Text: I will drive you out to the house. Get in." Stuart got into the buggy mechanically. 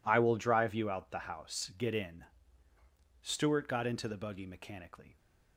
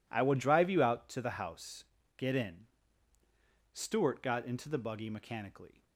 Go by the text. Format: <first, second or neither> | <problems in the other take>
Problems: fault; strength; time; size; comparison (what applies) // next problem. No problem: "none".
second | skips "to"; at 1.1 s